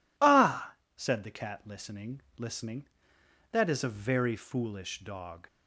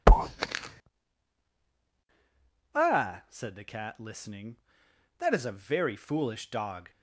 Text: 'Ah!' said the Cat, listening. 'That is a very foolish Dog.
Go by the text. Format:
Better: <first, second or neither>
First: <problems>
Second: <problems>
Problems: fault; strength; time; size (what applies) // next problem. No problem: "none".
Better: second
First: says "listening" twice; at 2.3 s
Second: none